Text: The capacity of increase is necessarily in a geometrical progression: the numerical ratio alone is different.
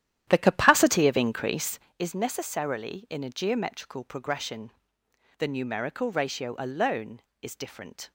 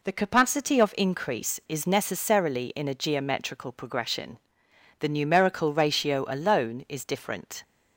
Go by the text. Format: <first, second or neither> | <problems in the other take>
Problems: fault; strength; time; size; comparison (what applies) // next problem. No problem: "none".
second | starts louder than the rest; strong; until 2.0 s; 11.5 dB